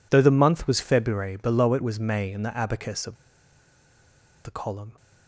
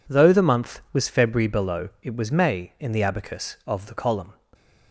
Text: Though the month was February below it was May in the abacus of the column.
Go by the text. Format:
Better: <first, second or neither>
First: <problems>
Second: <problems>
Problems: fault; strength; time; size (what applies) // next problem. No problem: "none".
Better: second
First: pauses between "of" and "the"; strong; at 3.1 s; 1.3 s long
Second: none